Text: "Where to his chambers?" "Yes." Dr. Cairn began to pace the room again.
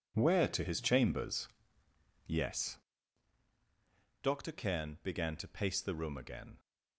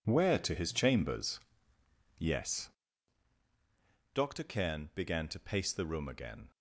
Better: neither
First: none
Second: none

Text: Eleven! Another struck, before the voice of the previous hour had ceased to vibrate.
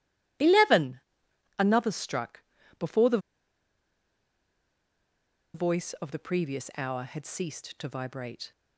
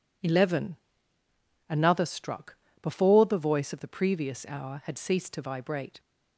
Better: second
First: pauses between "the" and "voice"; strong; at 3.1 s; 2.3 s long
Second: none

